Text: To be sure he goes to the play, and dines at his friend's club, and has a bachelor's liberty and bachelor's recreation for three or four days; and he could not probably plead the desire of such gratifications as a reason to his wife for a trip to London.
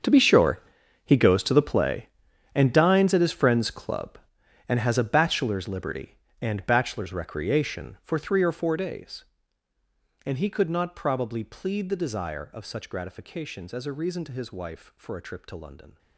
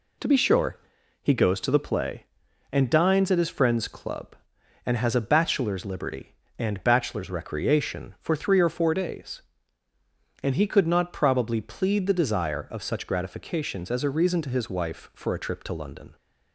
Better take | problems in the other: second | gets quieter; strong; throughout; 16 dB // pauses between "sure" and "he"; at 0.5 s; 0.44 s long; also in the second

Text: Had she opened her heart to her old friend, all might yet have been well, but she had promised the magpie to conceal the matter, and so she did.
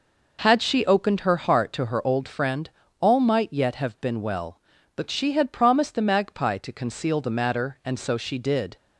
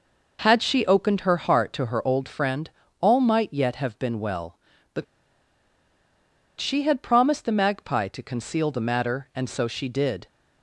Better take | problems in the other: first | pauses between "but" and "she"; strong; at 5.0 s; 1.5 s long

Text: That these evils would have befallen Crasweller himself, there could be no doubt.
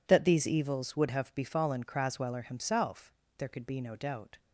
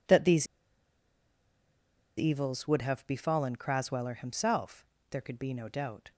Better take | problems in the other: first | pauses between "these" and "evils"; strong; at 0.4 s; 1.7 s long

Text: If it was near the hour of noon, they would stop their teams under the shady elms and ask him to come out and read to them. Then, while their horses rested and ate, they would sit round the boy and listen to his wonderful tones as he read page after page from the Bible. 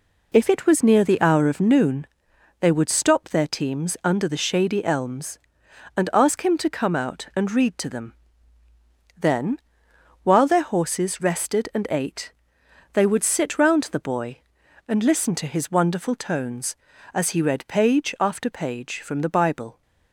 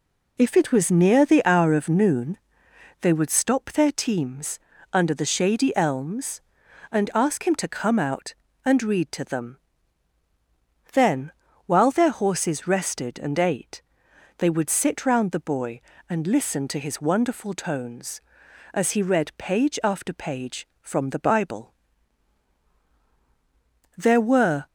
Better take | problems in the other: first | pauses between "teams" and "under"; slight; at 4.5 s; 0.34 s long // goes on to say "There were"; noticeable; from 23.9 s on; 0.68 s long

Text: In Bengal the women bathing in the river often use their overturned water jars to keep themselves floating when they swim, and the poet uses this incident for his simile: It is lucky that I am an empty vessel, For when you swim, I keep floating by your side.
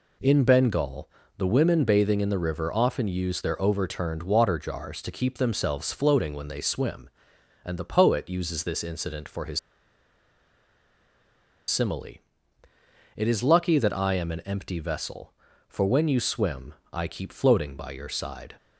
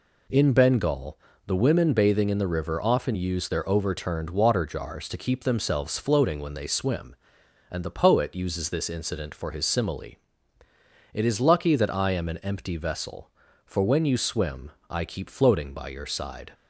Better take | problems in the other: second | pauses between "Bengal" and "the"; slight; at 1.0 s; 0.28 s long; slight in the second // pauses between "his" and "simile"; strong; at 9.5 s; 2.1 s long

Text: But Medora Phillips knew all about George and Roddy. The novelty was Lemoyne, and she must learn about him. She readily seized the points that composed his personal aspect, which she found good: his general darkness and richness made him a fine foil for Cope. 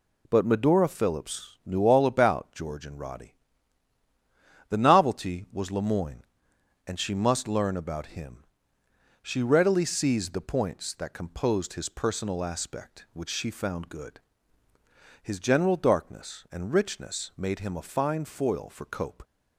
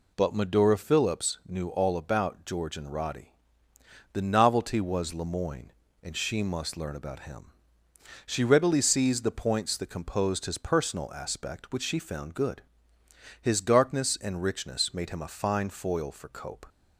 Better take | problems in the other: first | skips "general"; at 13.5 s

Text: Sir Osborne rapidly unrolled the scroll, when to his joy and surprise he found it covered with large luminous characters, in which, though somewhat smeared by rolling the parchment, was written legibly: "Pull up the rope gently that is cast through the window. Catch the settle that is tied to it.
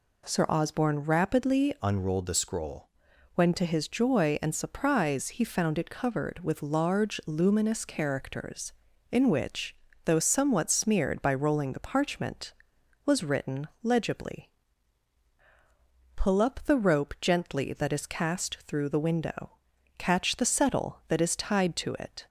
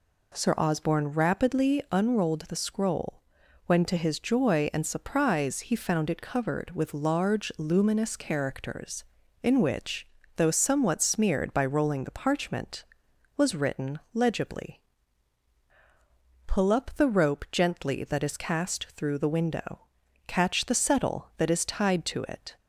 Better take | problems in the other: second | changes voice from "unrolled" to "scroll"; from 1.8 to 2.8 s; 1.0 s long // pauses between "written" and "legibly"; slight; at 13.6 s; 0.16 s long; slight in the second

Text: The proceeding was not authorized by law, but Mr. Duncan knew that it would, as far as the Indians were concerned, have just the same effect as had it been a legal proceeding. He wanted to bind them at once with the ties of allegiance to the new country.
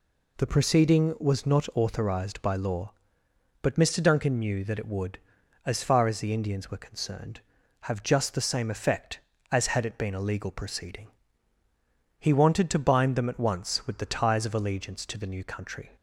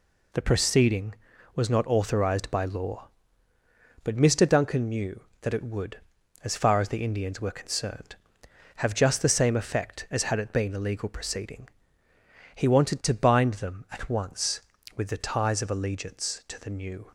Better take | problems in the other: first | stops before "country"; at 17.0 s

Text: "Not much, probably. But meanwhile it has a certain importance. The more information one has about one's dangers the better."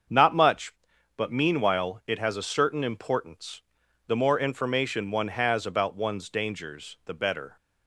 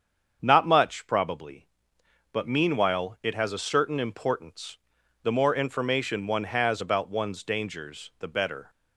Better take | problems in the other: second | starts louder than the rest; until 1.5 s; 7 dB; strong in the second // skips "probably"; at 0.9 s

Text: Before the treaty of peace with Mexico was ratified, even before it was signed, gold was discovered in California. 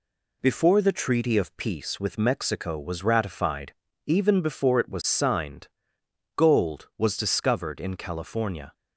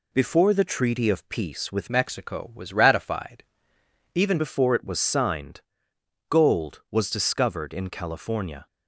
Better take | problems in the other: first | changes voice from "Mexico" to "even"; from 1.8 to 4.3 s; 2.5 s long

